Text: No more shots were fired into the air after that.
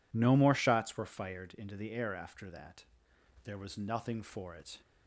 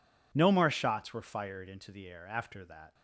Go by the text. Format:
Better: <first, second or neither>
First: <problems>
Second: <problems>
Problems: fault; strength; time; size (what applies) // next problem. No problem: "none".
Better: second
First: goes on to say "There was nothing for it"; from 3.4 s on; 1.3 s long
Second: none